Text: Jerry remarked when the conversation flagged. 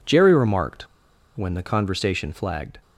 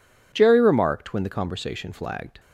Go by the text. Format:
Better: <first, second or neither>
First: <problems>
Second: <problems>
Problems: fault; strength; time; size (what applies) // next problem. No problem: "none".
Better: second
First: pauses between "remarked" and "when"; noticeable; at 0.8 s; 0.50 s long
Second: none